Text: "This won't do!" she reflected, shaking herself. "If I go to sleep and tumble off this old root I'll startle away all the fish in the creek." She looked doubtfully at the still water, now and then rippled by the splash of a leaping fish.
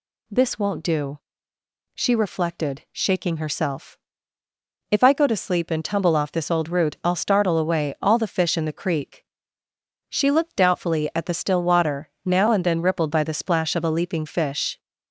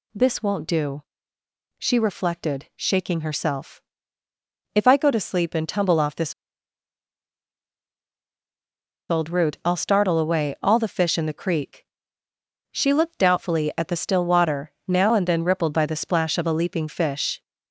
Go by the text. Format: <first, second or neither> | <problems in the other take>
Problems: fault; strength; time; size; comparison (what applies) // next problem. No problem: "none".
first | pauses between "this" and "old"; strong; at 6.3 s; 2.7 s long